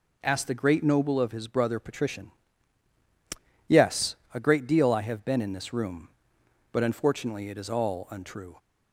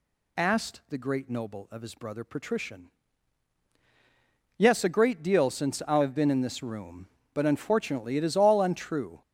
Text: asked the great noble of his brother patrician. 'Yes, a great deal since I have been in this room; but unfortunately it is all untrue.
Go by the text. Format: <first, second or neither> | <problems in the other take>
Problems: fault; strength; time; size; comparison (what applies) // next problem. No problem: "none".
second | skips "since"; at 4.9 s